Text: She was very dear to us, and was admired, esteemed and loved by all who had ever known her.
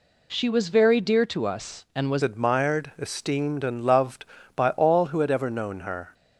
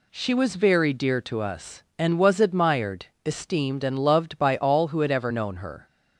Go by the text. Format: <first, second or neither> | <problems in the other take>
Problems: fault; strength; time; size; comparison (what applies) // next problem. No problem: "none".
second | changes voice at "admired"; from 2.2 s on; 3.9 s long